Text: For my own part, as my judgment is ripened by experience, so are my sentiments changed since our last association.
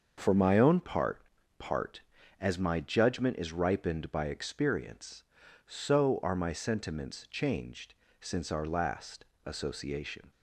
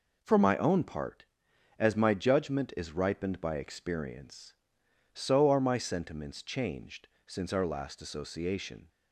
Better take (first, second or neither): second